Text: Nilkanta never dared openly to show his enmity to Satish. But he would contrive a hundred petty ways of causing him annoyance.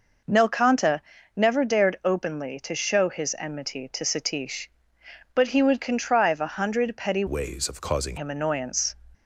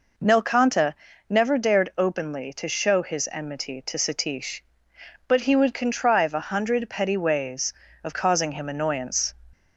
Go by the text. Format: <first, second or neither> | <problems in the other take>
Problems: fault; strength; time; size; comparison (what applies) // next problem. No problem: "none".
second | pauses between "Nilkanta" and "never"; slight; at 1.0 s; 0.34 s long; slight in the second // changes voice from "ways" to "causing"; from 7.2 to 8.1 s; 0.9 s long